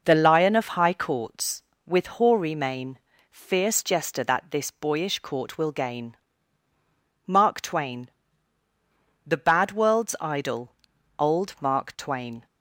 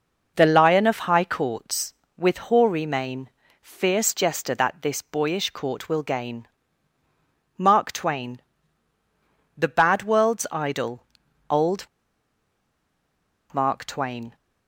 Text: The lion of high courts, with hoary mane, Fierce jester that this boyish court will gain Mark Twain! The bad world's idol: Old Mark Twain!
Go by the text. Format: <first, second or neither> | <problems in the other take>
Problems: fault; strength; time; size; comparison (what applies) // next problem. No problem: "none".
first | pauses between "gain" and "Mark"; at 6.4 s; 1.0 s long; also in the first // pauses between "Old" and "Mark"; strong; at 11.8 s; 1.6 s long